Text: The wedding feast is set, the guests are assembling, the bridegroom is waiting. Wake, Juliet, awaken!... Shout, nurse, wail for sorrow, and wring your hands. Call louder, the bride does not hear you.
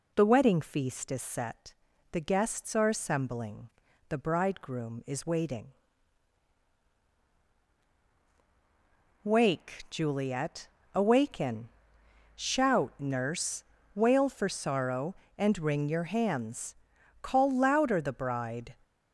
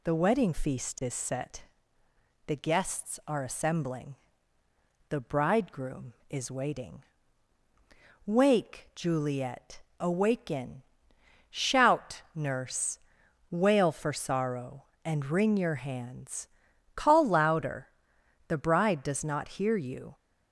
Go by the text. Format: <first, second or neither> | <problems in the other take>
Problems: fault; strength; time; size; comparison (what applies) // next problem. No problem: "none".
second | stops before "does not hear you"; at 18.8 s